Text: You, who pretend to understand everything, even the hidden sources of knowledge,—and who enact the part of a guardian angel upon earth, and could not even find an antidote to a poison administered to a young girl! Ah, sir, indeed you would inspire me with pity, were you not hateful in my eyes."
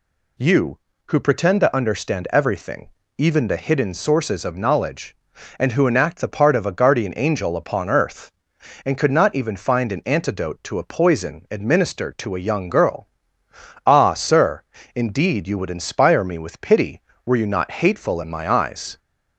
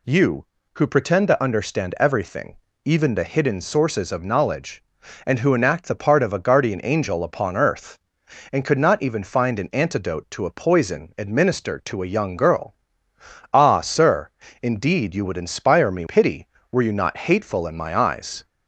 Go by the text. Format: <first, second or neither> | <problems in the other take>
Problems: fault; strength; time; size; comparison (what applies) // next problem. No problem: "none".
first | skips "with"; at 16.0 s